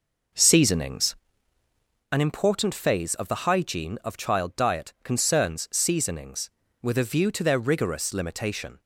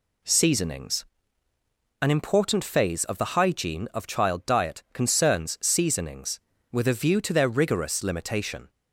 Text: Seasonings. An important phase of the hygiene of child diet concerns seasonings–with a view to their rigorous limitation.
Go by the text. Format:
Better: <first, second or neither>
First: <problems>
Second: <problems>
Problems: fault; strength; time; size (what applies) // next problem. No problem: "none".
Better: second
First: starts louder than the rest; noticeable; until 2.1 s; 5 dB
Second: none